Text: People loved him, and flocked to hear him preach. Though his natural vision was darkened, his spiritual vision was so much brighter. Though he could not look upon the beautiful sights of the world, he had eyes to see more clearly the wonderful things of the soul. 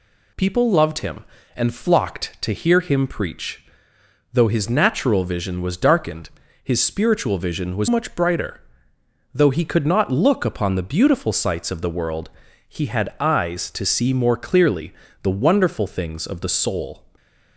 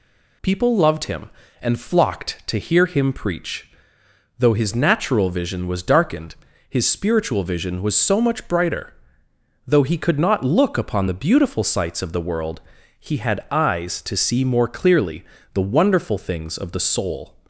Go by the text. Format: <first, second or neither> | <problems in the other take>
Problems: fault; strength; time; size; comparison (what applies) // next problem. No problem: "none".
second | skips "so"; at 7.8 s // pauses between "clearly" and "the"; slight; at 14.9 s; 0.28 s long; slight in the second